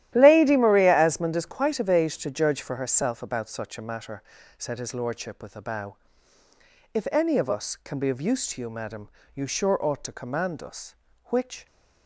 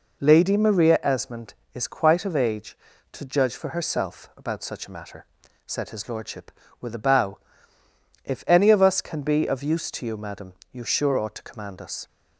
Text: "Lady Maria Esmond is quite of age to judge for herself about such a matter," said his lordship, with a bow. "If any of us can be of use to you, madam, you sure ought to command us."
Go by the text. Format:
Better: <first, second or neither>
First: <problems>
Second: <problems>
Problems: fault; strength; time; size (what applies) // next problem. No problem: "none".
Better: second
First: starts louder than the rest; strong; until 1.1 s; 12.5 dB // goes on to say "Which"; slight; from 11.3 s on; 0.34 s long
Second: none